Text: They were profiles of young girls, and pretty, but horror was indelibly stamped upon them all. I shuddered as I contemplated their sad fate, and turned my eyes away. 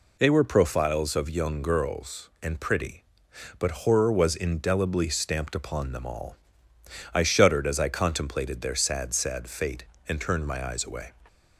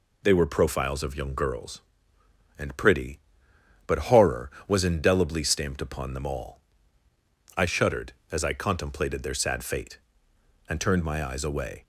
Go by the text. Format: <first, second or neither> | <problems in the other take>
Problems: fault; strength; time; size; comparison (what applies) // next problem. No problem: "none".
second | says "sad" twice; at 9.1 s